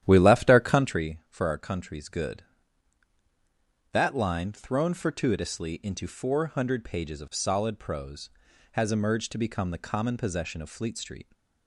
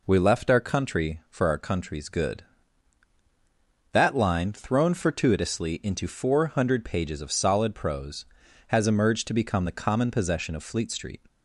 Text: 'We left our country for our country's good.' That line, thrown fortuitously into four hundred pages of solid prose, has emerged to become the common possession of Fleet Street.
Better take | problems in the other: second | starts louder than the rest; strong; until 1.0 s; 11 dB

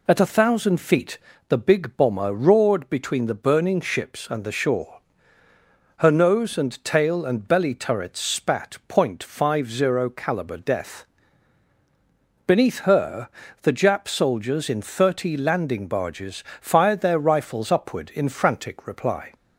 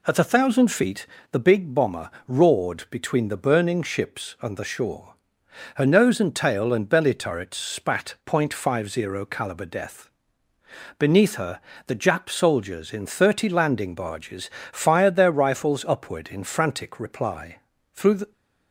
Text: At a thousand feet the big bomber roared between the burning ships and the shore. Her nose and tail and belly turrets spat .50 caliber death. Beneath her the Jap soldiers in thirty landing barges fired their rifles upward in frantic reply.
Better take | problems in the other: first | pauses between "feet" and "the"; slight; at 1.0 s; 0.24 s long; slight in the first // pauses between "bomber" and "roared"; slight; at 2.1 s; 0.16 s long // pauses between "her" and "the"; slight; at 11.6 s; 0.26 s long; slight in the first // pauses between "barges" and "fired"; slight; at 14.5 s; 0.22 s long; slight in the first // goes on to say "Through the"; slight; from 17.9 s on; 0.38 s long

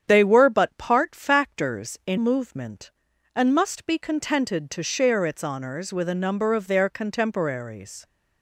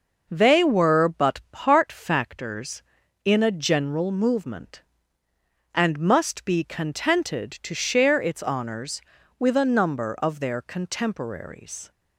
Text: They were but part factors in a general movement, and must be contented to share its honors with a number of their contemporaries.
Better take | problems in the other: second | starts louder than the rest; strong; until 1.0 s; 8.5 dB // skips "a general"; at 2.1 s

